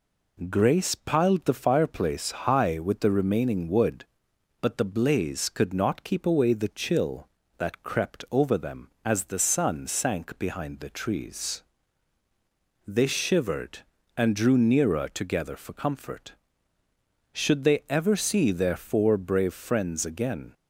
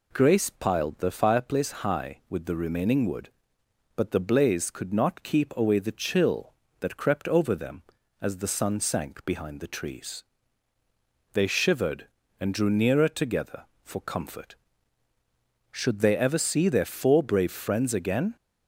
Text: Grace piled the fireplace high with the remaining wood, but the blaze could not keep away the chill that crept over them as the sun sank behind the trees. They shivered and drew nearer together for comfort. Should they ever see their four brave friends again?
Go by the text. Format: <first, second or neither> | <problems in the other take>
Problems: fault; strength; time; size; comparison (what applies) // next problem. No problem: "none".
neither | none